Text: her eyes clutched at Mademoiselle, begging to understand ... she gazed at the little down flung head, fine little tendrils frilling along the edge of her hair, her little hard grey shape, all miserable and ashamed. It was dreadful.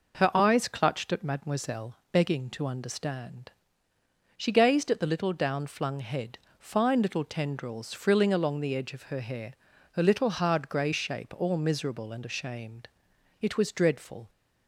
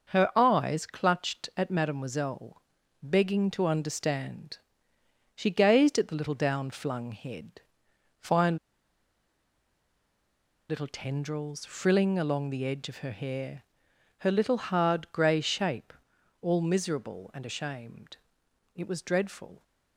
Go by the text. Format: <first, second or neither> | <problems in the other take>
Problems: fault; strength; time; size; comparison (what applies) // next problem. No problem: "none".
first | pauses between "fine" and "little"; strong; at 8.5 s; 2.1 s long